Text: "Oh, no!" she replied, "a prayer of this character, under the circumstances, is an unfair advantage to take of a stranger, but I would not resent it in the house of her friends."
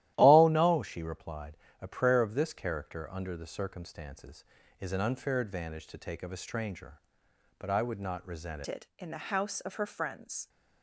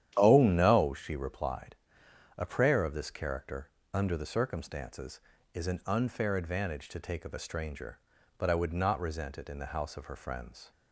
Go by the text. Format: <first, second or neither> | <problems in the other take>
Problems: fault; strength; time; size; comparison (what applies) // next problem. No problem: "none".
second | starts louder than the rest; strong; until 1.1 s; 13.5 dB; strong in the second // changes voice at "it"; from 8.6 s on; 1.8 s long